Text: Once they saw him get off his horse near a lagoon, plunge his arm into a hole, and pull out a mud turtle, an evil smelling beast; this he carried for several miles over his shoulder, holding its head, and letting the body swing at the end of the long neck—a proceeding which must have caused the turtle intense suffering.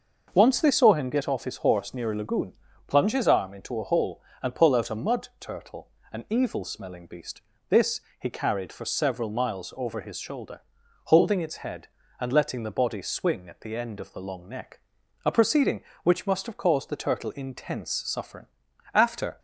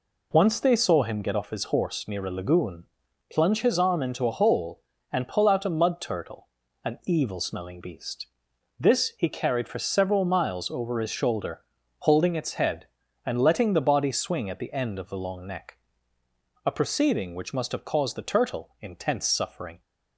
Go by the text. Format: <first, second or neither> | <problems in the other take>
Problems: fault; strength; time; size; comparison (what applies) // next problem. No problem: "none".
second | starts louder than the rest; until 1.3 s; 6 dB // pauses between "this" and "he"; slight; at 8.0 s; 0.18 s long // goes on to say "After"; slight; from 18.9 s on; 0.46 s long